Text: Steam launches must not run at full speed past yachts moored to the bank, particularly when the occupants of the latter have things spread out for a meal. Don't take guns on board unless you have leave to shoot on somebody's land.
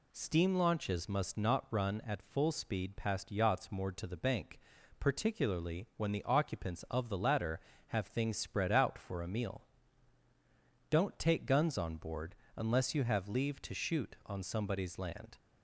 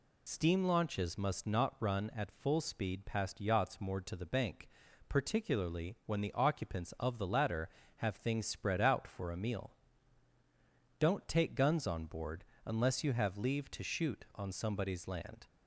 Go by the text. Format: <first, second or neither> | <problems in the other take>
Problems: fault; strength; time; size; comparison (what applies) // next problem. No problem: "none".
first | loses the start of "Steam"; at 0.2 s; 55 ms // pauses between "board" and "unless"; slight; at 12.4 s; 0.22 s long; slight in the first